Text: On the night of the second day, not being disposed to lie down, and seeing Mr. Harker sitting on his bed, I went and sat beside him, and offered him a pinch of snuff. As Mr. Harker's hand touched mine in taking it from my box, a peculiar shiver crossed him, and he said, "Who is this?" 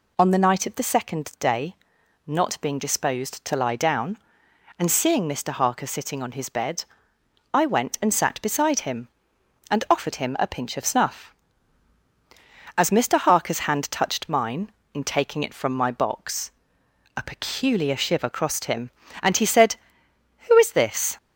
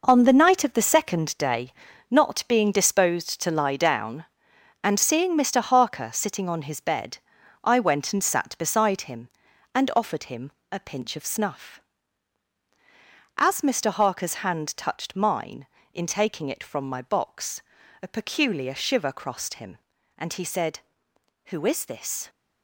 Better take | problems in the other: first | gets quieter; strong; throughout; 10 dB // pauses between "him" and "a"; slight; at 10.5 s; 0.20 s long

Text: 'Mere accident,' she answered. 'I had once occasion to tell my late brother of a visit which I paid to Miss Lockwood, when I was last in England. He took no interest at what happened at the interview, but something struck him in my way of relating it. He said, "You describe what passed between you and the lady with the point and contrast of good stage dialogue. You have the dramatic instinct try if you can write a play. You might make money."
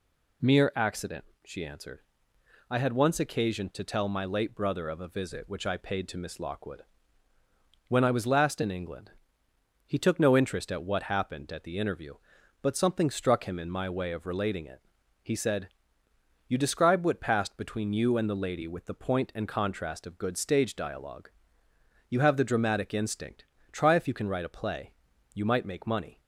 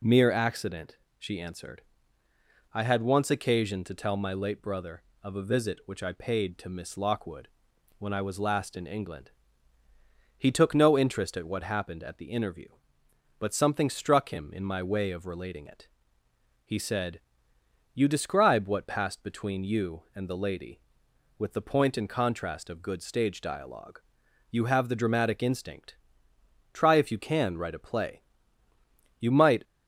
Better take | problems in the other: first | pauses between "instinct" and "try"; noticeable; at 25.9 s; 0.78 s long; slight in the first // stops before "make money"; at 29.6 s

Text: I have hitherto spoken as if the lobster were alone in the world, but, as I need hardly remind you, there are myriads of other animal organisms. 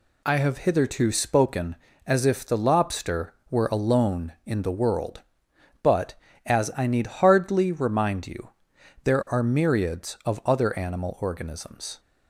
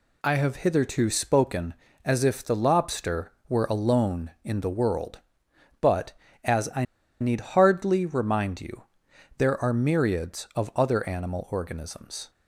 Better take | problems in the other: first | pauses between "I" and "need"; at 6.8 s; 0.36 s long

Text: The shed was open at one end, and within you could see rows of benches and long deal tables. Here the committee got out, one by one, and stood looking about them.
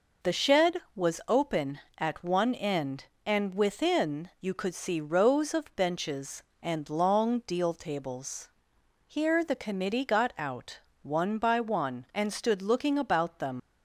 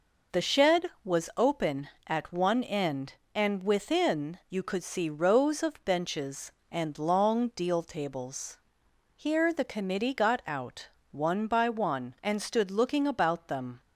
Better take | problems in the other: second | leaves "them" unfinished; at 13.5 s; 110 ms

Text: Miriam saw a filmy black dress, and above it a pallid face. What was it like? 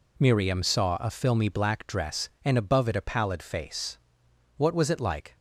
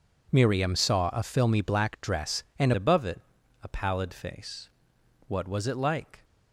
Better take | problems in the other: first | changes voice at "above"; from 2.7 s on; 3.5 s long // pauses between "it" and "a"; at 3.2 s; 0.40 s long

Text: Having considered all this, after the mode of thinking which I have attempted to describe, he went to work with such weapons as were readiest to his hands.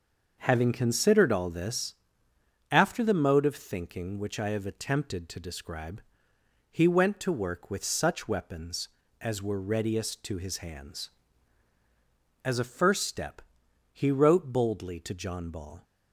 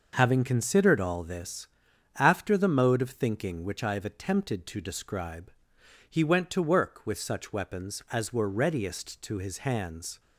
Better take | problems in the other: second | starts louder than the rest; until 1.3 s; 6 dB // goes on to say "As a first step he wrote boldly to John Ball"; strong; from 12.4 s on; 3.3 s long

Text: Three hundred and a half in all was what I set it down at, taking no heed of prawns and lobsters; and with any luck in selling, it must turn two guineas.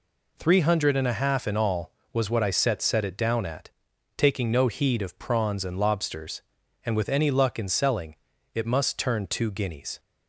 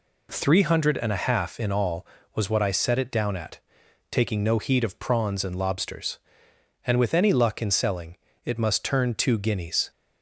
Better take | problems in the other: second | says "set" twice; at 2.8 s

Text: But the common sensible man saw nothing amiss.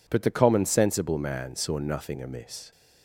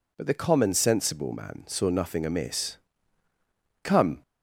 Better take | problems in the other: first | goes on to say "Come"; slight; from 3.8 s on; 0.40 s long

